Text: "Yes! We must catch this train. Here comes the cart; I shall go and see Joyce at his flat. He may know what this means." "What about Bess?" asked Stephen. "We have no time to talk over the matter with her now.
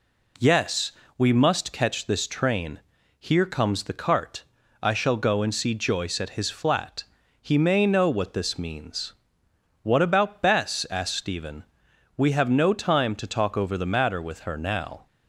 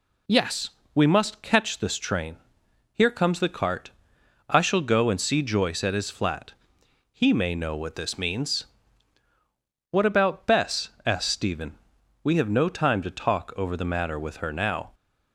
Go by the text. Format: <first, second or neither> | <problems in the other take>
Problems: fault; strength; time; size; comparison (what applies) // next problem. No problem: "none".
neither | none